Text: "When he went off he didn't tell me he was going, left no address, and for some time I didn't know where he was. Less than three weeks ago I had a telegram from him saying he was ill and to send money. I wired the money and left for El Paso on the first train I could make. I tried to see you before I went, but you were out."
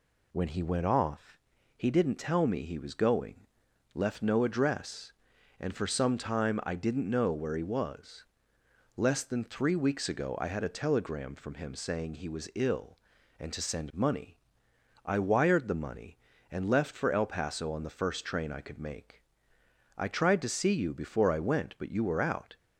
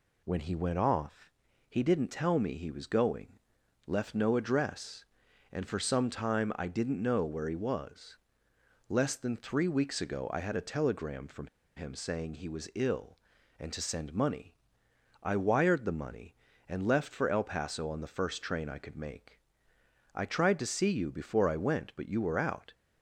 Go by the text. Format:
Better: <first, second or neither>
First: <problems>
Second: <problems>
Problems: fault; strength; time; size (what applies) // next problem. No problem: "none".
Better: first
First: pauses between "off" and "he"; at 1.3 s; 0.38 s long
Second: pauses between "off" and "he"; at 1.2 s; 0.38 s long // pauses between "from" and "him"; slight; at 11.4 s; 0.28 s long